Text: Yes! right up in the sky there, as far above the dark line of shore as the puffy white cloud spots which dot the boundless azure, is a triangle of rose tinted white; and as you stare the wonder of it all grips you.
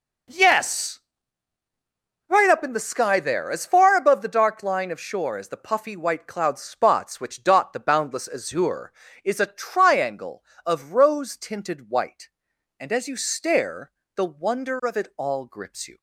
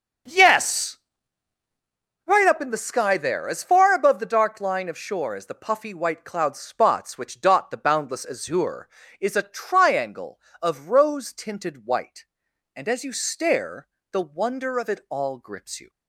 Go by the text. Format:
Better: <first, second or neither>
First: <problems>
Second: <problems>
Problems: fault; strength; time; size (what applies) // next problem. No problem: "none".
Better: first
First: pauses between "stare" and "the"; slight; at 13.9 s; 0.26 s long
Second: starts louder than the rest; until 1.9 s; 7 dB // pauses between "stare" and "the"; slight; at 13.8 s; 0.26 s long